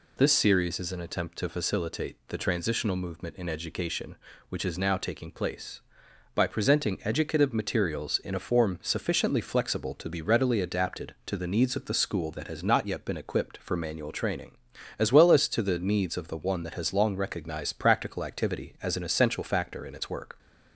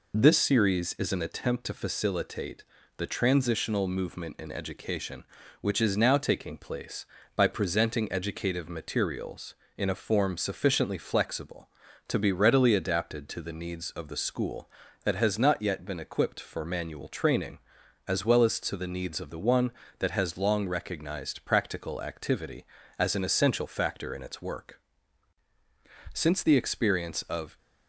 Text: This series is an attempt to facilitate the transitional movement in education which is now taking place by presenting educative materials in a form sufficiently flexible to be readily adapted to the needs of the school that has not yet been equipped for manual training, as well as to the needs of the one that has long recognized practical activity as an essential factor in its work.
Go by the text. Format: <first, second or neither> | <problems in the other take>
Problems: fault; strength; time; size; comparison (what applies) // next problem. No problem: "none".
first | pauses between "facilitate" and "the"; slight; at 2.6 s; 0.32 s long // goes on to say "Since the experience of"; from 26.1 s on; 1.4 s long